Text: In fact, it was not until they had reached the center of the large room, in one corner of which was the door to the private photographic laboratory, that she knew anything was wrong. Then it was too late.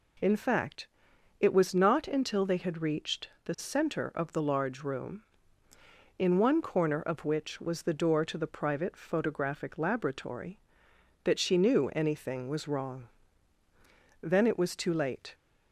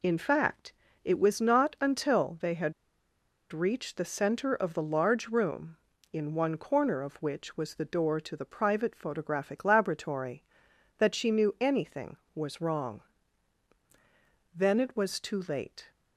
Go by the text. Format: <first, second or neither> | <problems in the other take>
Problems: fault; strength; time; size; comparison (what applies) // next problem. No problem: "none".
first | pauses between "had" and "reached"; noticeable; at 2.7 s; 0.79 s long